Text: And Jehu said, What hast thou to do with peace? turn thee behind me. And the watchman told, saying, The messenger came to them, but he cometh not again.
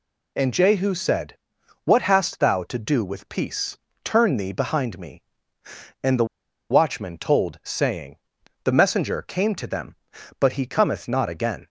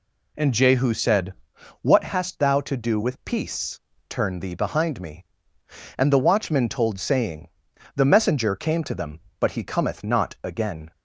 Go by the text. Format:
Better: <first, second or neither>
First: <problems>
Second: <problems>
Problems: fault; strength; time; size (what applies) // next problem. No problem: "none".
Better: second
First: pauses between "the" and "watchman"; at 6.2 s; 0.45 s long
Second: none